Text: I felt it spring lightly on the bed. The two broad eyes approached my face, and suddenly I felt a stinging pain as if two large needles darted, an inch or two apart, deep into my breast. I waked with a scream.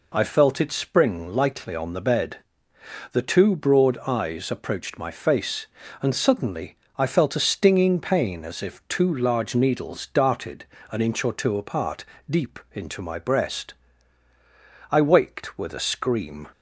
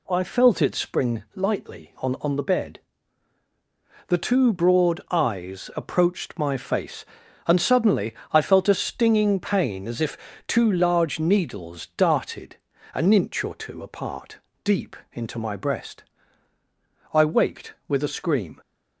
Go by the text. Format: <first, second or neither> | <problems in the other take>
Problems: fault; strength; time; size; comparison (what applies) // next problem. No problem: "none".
first | says "on" twice; at 2.2 s // pauses between "suddenly" and "I"; slight; at 8.1 s; 0.18 s long; slight in the first // pauses between "if" and "two"; slight; at 10.1 s; 0.30 s long // pauses between "deep" and "into"; slight; at 14.9 s; 0.18 s long